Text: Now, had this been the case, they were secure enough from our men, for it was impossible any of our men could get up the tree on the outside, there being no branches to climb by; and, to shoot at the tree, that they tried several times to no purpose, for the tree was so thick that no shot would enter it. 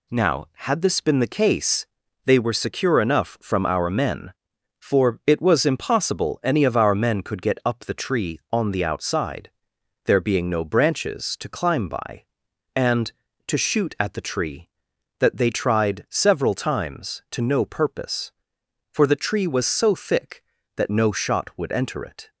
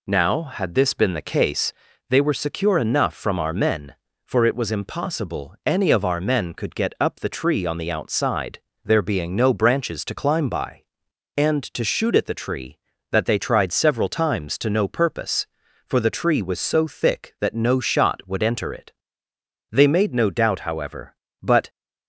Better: first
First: none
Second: goes on to say "They made no doubt however but"; strong; from 19.7 s on; 1.9 s long

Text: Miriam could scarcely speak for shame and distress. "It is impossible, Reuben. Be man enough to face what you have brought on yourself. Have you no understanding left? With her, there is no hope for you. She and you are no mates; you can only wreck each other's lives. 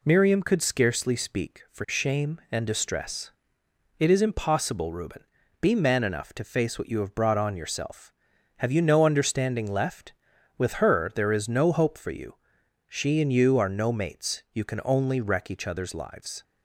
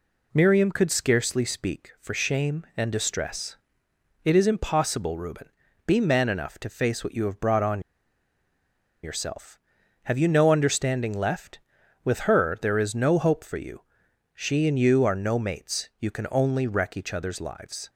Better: first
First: none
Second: pauses between "on" and "yourself"; at 7.8 s; 1.2 s long

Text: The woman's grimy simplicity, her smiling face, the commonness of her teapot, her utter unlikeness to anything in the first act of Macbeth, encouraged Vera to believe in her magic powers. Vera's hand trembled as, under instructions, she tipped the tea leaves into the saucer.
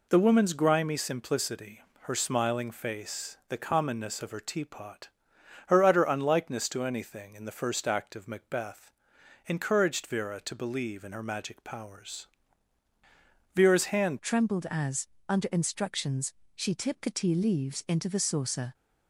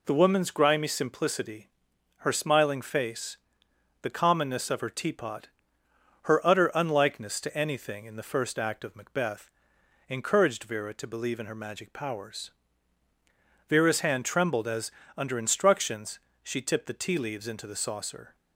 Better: second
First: changes voice at "trembled"; from 14.2 s on; 4.5 s long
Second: none

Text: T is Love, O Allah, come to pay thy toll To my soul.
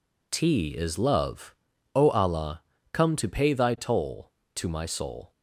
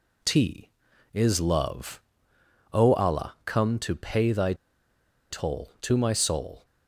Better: first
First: none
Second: pauses between "thy" and "toll"; noticeable; at 4.5 s; 0.76 s long

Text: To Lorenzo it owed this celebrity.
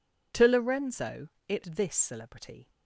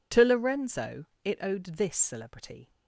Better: second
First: pauses between "Lorenzo" and "it"; slight; at 1.2 s; 0.22 s long // skips "owed"; at 1.6 s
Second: pauses between "Lorenzo" and "it"; slight; at 1.0 s; 0.21 s long

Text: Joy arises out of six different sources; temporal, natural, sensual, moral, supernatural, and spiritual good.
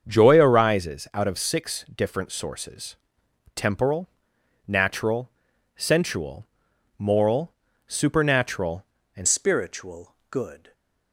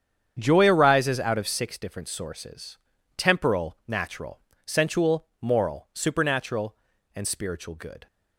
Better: second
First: starts louder than the rest; until 1.1 s; 7 dB // changes voice at "spiritual"; from 9.2 s on; 1.5 s long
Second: starts louder than the rest; strong; until 1.3 s; 8 dB

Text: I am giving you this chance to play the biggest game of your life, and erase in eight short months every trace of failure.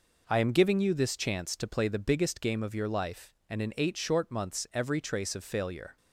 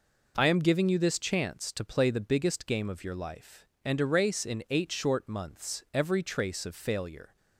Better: second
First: skips "erase"; at 3.6 s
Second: none

